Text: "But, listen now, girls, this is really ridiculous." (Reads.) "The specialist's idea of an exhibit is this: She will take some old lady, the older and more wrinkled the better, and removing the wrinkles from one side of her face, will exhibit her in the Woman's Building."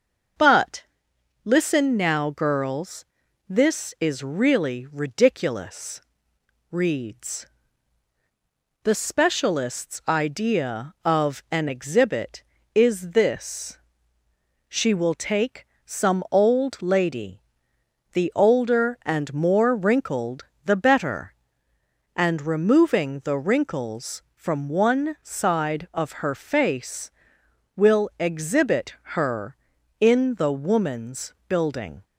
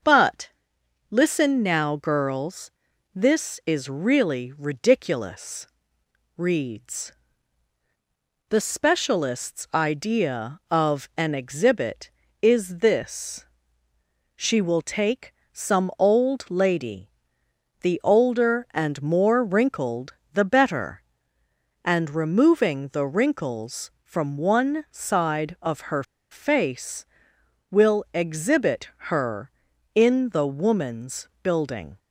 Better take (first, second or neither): first